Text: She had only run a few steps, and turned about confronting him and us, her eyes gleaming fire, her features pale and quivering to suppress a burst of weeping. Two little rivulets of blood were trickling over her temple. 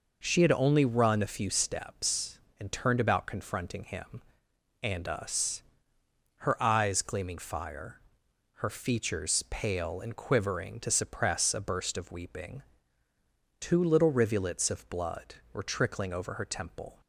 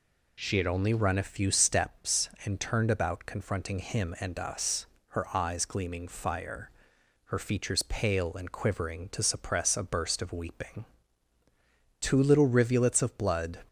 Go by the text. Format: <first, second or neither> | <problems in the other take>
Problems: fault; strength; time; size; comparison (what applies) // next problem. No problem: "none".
first | stops before "were trickling over her temple"; at 13.6 s